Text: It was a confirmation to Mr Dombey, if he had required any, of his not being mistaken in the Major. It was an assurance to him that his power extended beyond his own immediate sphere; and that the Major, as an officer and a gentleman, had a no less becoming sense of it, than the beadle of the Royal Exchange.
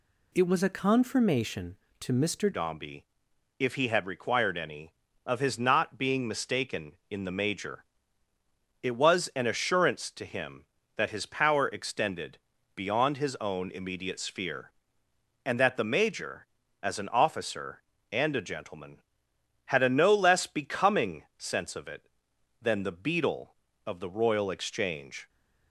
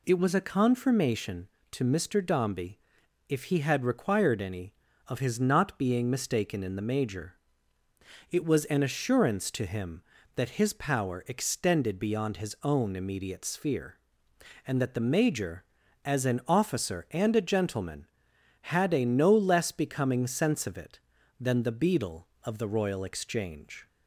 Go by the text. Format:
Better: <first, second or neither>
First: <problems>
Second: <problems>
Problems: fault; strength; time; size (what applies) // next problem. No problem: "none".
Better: second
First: changes voice at "Dombey"; from 2.5 s on; 22.7 s long // pauses between "extended" and "beyond"; slight; at 12.3 s; 0.36 s long // pauses between "becoming" and "sense"; slight; at 21.2 s; 0.16 s long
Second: none